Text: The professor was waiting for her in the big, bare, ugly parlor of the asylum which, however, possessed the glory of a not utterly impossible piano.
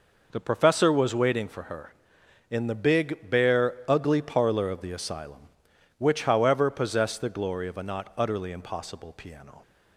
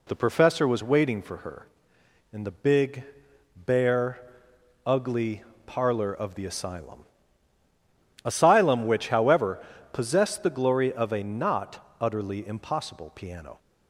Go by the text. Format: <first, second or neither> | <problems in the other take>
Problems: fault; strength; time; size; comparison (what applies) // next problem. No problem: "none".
first | pauses between "ugly" and "parlor"; slight; at 5.4 s; 0.22 s long // says "asylum" twice; at 8.2 s